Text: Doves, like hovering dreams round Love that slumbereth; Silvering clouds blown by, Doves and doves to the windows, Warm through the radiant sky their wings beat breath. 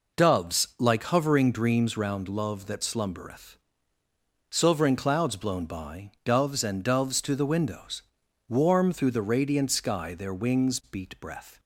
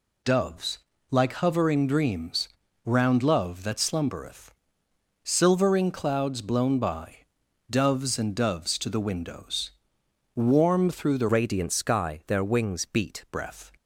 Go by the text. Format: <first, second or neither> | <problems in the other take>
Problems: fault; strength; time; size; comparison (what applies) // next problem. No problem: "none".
first | pauses between "dreams" and "round"; at 2.4 s; 0.38 s long // changes voice from "radiant" to "beat"; from 11.3 to 13.2 s; 1.9 s long